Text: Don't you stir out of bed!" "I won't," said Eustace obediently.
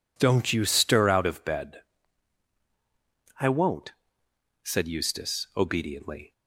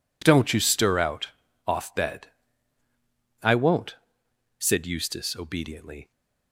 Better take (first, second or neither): first